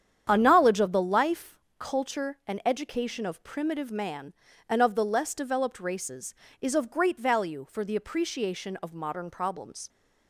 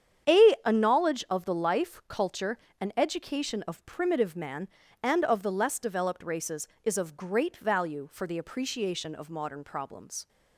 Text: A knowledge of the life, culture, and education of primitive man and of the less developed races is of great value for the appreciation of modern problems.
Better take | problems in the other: first | starts louder than the rest; strong; until 1.4 s; 8.5 dB; strong in the first // says "A" twice; at 0.6 s

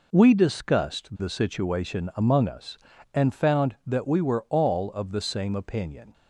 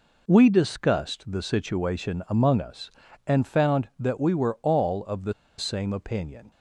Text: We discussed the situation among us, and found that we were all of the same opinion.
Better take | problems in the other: first | pauses between "the" and "same"; slight; at 5.3 s; 0.27 s long

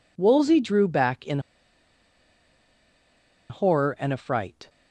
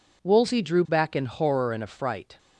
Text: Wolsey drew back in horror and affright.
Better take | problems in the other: second | pauses between "in" and "horror"; strong; at 1.3 s; 2.1 s long

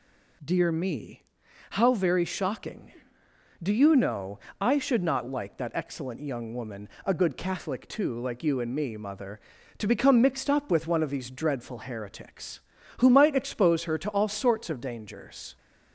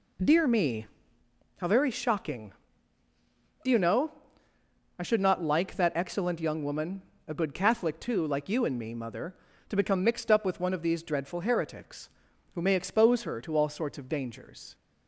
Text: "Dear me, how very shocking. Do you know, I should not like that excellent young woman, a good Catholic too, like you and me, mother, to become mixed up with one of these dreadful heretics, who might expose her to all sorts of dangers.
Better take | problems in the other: first | says "may" for "might"; at 12.6 s

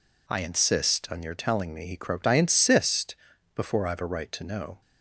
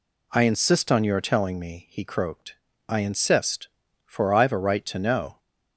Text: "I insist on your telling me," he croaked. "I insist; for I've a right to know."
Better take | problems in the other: second | says "before" for "for"; at 3.5 s

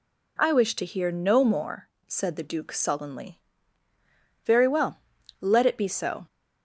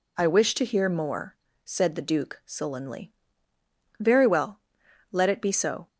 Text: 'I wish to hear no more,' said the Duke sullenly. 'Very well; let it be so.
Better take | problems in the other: first | skips "no"; at 0.8 s

